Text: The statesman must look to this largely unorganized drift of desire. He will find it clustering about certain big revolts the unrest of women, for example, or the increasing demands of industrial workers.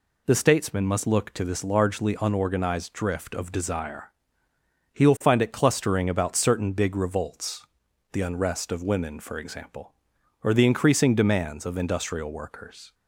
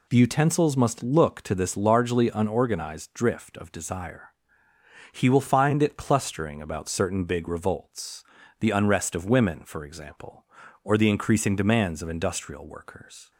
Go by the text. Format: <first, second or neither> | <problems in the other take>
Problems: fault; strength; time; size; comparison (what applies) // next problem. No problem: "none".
first | says "utensils" for "statesman"; at 0.1 s // pauses between "revolts" and "the"; at 8.2 s; 0.38 s long; noticeable in the first